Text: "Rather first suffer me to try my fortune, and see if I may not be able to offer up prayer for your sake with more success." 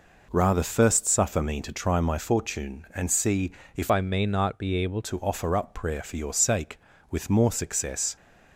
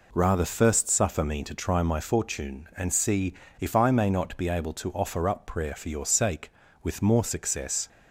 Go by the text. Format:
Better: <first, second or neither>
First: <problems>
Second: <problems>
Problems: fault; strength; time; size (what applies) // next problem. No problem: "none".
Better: second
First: pauses between "see" and "if"; slight; at 3.5 s; 0.26 s long // changes voice from "I" to "able"; from 3.9 to 5.0 s; 1.1 s long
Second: pauses between "see" and "if"; slight; at 3.3 s; 0.27 s long